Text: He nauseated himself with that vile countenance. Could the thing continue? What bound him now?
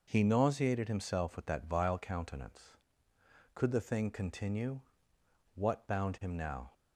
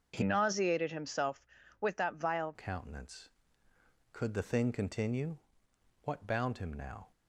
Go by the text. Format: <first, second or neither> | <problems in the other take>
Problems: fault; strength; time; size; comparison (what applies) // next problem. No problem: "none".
first | starts louder than the rest; until 1.1 s; 6.5 dB // changes voice from "nauseated" to "vile"; from 0.2 to 2.5 s; 2.3 s long